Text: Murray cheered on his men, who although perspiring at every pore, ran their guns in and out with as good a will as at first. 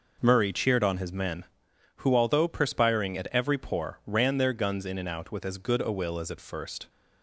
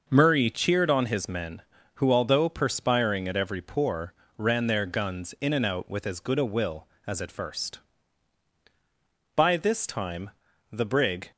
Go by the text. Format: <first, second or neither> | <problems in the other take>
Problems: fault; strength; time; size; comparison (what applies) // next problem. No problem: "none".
first | starts louder than the rest; noticeable; until 1.0 s; 6 dB // goes on to say "By this time the brig"; strong; from 9.3 s on; 1.9 s long